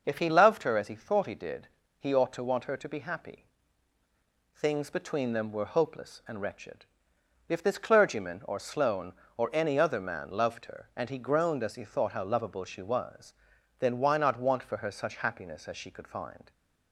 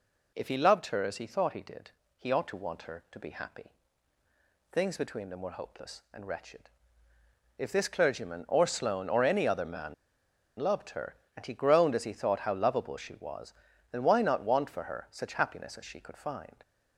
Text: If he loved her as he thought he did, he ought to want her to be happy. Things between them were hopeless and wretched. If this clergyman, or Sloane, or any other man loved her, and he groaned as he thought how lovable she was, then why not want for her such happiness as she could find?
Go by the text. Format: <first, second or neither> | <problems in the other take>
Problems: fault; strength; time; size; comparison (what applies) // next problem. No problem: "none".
first | pauses between "man" and "loved"; noticeable; at 9.9 s; 0.64 s long